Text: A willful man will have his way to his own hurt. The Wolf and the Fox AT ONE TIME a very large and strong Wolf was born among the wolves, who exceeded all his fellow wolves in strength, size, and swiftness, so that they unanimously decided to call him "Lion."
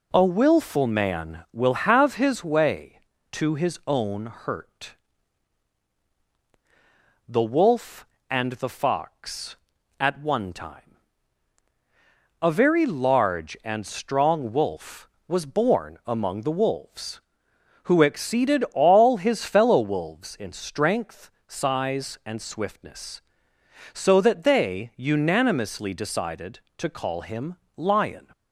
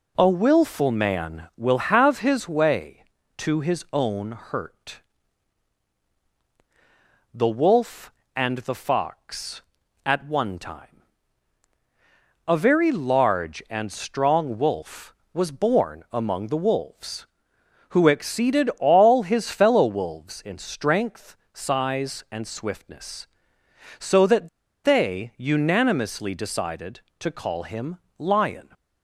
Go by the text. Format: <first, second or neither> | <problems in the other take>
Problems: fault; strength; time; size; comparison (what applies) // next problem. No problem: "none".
first | pauses between "TIME" and "a"; strong; at 11.0 s; 1.4 s long; strong in the first // pauses between "that" and "they"; slight; at 24.4 s; 0.36 s long // pauses between "him" and "Lion"; slight; at 27.9 s; 0.18 s long; slight in the first